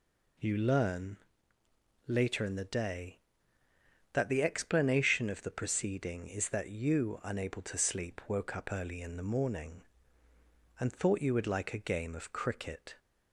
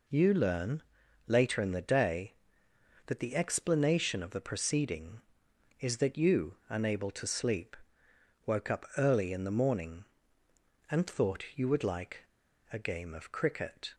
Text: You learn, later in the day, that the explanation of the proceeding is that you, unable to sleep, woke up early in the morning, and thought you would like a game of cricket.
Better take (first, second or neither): first